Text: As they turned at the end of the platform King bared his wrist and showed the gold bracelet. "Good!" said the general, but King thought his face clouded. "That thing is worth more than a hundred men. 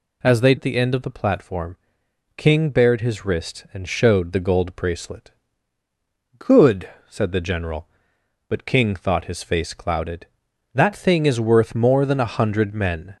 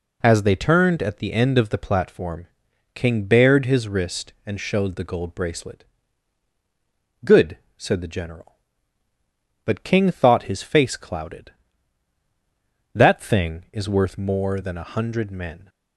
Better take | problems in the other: second | skips "turned"; at 0.5 s // pauses between "platform" and "King"; noticeable; at 1.7 s; 0.60 s long; noticeable in the second

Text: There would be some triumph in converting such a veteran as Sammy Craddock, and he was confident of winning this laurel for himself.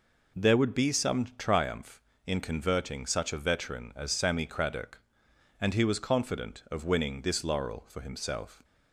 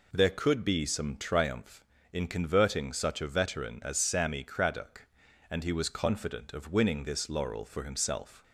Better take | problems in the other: first | says "could" for "would"; at 0.3 s

